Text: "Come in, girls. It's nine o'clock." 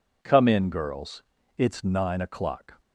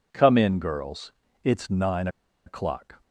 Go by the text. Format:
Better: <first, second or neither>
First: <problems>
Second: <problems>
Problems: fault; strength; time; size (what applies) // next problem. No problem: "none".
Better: first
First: none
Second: pauses between "nine" and "o'clock"; at 2.0 s; 0.37 s long